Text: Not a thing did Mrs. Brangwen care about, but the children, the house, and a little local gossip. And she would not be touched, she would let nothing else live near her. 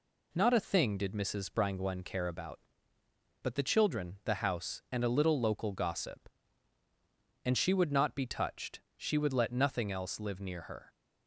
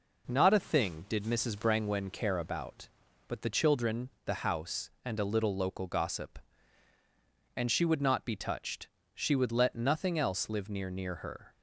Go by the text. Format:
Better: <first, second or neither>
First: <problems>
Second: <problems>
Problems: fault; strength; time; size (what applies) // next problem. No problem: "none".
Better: first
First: none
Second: says "near" twice; at 10.8 s